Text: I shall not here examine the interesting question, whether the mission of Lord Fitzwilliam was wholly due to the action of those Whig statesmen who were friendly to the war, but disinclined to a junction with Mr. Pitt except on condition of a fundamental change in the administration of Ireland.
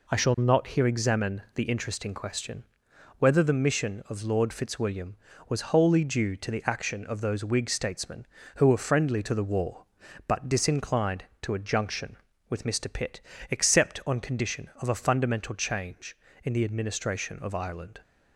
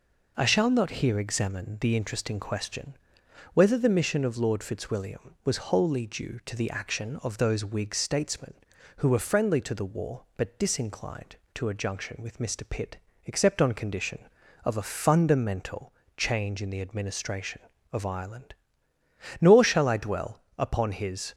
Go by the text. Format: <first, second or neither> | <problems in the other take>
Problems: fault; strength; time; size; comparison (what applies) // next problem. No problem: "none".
first | pauses between "Pitt" and "except"; slight; at 12.9 s; 0.28 s long; slight in the first // pauses between "fundamental" and "change"; slight; at 15.9 s; 0.24 s long // goes on to say "Nor shall I dwell upon his"; strong; from 19.3 s on; 1.9 s long